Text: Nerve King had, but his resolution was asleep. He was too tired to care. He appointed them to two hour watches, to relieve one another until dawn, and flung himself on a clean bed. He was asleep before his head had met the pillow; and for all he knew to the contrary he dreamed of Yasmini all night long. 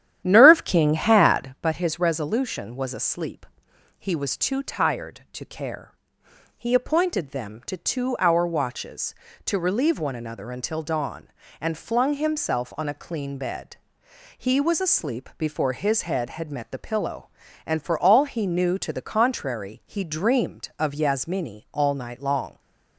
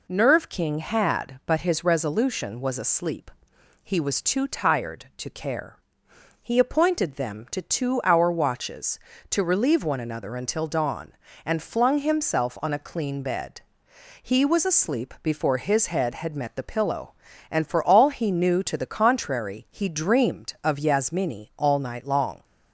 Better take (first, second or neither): second